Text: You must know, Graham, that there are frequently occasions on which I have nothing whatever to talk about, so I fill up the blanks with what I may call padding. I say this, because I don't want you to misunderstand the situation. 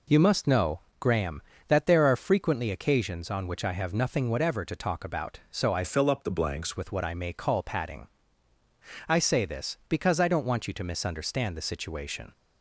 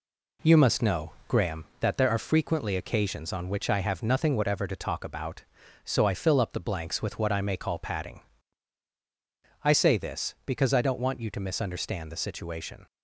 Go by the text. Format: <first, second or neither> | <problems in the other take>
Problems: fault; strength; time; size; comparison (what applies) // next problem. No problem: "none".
second | changes voice from "fill" to "blanks"; from 5.8 to 6.7 s; 0.9 s long